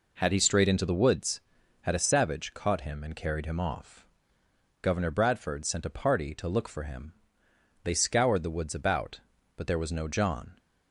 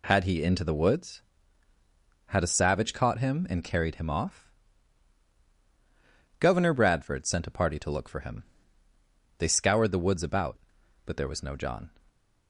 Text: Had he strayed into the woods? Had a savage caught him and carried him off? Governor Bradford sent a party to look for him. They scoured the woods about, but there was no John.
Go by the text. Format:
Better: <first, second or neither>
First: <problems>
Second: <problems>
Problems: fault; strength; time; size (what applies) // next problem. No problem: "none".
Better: first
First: none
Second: skips "strayed"; at 0.4 s